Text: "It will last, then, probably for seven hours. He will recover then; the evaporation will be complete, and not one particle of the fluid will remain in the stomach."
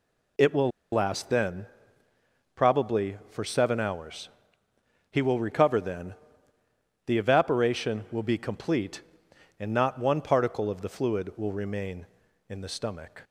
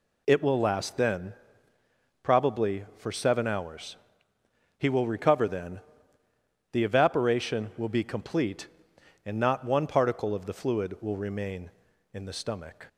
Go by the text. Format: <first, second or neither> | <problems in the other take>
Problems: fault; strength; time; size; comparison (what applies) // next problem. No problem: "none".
second | pauses between "will" and "last"; slight; at 0.7 s; 0.22 s long